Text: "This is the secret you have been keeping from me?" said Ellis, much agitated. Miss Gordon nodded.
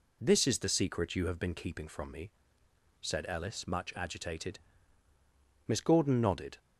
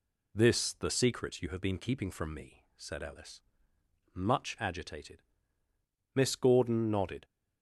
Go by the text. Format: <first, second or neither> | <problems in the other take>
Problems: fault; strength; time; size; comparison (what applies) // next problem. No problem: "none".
first | skips "is"; at 0.7 s